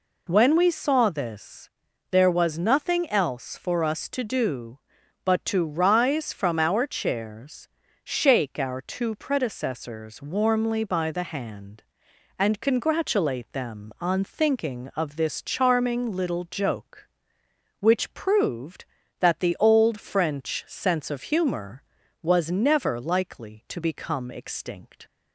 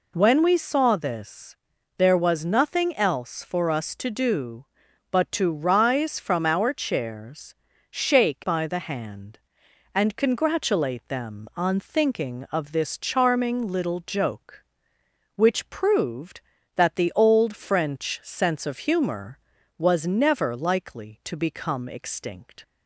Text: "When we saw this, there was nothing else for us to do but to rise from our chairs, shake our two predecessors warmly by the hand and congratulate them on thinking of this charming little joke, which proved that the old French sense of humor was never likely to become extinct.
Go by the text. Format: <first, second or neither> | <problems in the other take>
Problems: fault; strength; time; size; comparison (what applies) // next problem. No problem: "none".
first | skips "our two predecessors warmly"; at 8.4 s